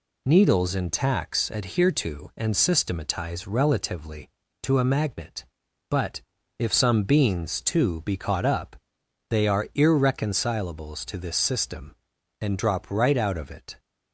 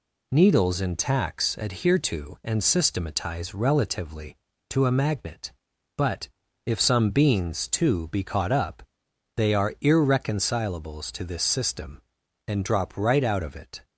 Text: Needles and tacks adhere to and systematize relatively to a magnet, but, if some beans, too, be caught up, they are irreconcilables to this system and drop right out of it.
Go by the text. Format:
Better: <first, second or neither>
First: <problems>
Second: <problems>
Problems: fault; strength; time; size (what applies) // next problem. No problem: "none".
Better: neither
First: none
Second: none